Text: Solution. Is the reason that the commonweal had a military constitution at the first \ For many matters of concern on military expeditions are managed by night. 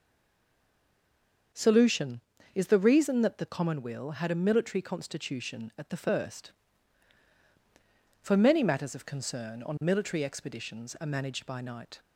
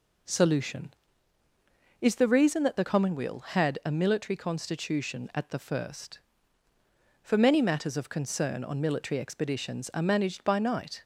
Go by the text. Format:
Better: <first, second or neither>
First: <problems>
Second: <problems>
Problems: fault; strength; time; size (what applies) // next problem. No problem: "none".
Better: second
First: stays silent before the first word; noticeable; until 1.5 s; 1.5 s long // starts louder than the rest; until 2.8 s; 6.5 dB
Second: none